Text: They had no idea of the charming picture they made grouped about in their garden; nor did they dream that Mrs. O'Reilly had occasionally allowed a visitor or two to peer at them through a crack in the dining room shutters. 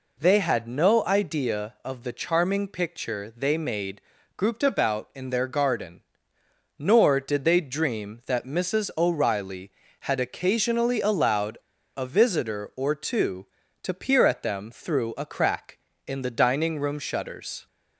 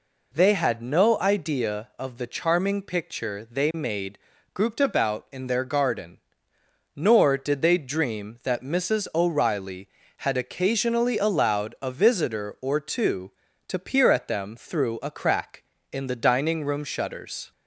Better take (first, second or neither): second